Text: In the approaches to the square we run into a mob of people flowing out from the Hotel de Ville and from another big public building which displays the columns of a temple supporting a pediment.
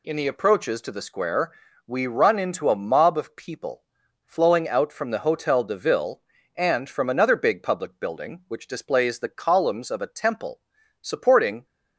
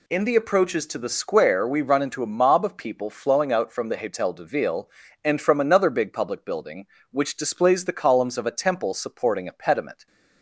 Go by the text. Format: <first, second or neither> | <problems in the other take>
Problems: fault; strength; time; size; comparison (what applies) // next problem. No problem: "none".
second | pauses between "square" and "we"; slight; at 1.5 s; 0.36 s long // pauses between "people" and "flowing"; at 3.8 s; 0.42 s long // pauses between "temple" and "supporting"; at 10.5 s; 0.42 s long // stops before "a pediment"; at 11.6 s